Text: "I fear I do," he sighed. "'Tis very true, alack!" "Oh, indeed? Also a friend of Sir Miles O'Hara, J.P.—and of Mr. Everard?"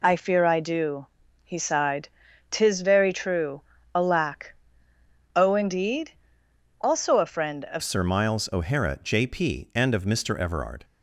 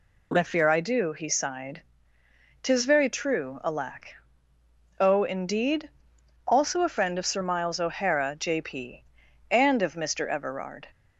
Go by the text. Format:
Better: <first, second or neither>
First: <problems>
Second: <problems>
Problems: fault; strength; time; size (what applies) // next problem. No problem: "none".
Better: second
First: changes voice at "Sir"; from 7.8 s on; 3.0 s long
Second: none